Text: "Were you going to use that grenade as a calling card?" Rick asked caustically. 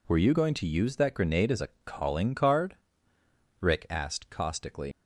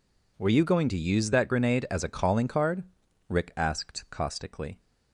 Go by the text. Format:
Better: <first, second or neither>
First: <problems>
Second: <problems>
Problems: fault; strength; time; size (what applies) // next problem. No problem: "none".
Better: second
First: pauses between "a" and "calling"; slight; at 1.6 s; 0.16 s long // leaves "caustically" unfinished; at 4.9 s; 95 ms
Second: none